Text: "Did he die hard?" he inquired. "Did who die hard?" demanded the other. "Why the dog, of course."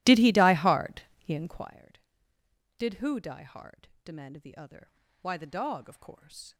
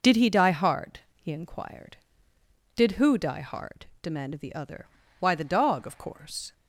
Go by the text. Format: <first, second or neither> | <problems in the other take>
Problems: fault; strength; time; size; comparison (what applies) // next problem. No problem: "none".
second | starts louder than the rest; strong; until 1.7 s; 16 dB